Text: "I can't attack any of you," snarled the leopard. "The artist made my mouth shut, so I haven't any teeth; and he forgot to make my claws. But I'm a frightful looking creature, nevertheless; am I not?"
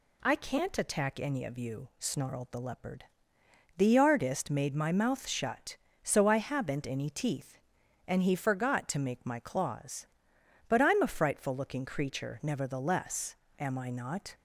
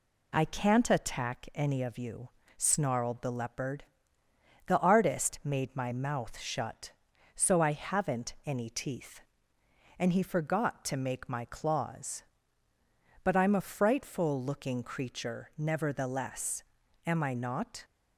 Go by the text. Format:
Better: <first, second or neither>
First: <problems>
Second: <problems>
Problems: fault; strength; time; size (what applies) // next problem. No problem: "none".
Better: neither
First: none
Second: none